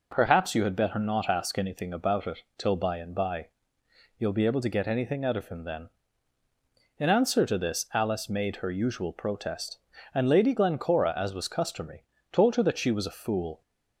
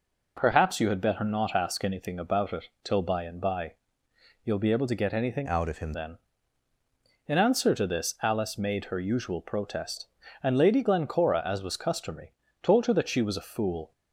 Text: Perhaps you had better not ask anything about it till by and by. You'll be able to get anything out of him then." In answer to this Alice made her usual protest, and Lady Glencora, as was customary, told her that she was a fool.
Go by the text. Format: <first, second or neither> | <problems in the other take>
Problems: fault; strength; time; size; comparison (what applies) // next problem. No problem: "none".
first | pauses between "it" and "till"; slight; at 2.6 s; 0.18 s long; slight in the first // changes voice from "out" to "him"; from 5.4 to 5.9 s; 0.5 s long